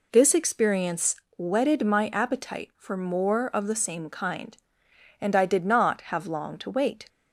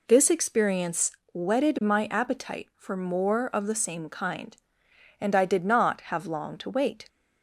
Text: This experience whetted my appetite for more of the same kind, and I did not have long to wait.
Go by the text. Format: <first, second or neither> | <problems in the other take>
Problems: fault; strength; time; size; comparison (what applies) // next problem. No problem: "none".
neither | pauses between "experience" and "whetted"; slight; the same in both